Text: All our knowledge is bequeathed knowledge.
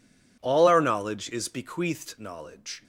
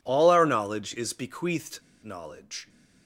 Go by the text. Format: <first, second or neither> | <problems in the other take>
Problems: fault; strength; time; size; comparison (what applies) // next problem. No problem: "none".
first | pauses between "bequeathed" and "knowledge"; slight; at 1.8 s; 0.21 s long